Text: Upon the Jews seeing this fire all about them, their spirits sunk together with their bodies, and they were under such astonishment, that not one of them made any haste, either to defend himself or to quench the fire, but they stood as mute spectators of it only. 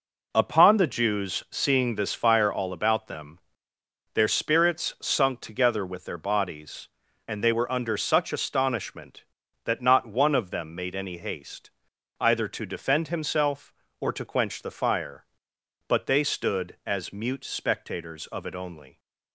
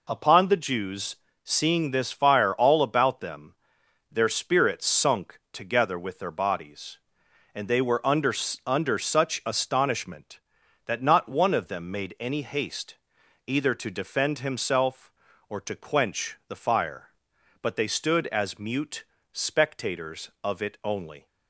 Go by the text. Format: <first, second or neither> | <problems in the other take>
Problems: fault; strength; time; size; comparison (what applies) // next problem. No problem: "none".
first | pauses between "Jews" and "seeing"; slight; at 1.1 s; 0.28 s long // says "under" twice; at 8.6 s // pauses between "mute" and "spectators"; slight; at 19.0 s; 0.30 s long